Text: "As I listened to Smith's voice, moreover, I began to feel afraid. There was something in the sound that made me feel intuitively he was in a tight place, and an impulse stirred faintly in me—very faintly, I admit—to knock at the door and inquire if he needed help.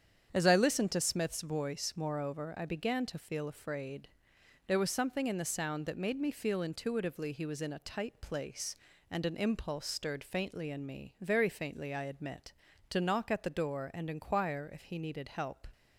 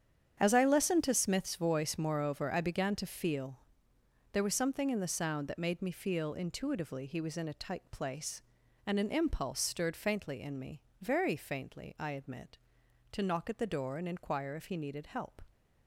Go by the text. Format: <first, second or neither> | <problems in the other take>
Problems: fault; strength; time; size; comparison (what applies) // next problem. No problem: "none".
first | starts louder than the rest; strong; until 1.4 s; 8.5 dB; strong in the first // skips "afraid"; at 3.9 s